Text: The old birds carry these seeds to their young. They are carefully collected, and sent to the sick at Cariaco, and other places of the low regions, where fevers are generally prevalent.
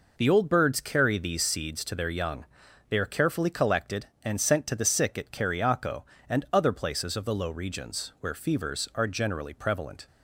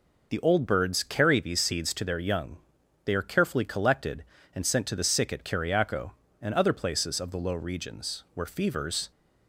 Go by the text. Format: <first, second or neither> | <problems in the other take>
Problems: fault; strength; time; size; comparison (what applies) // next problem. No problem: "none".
first | stops before "are generally prevalent"; at 9.1 s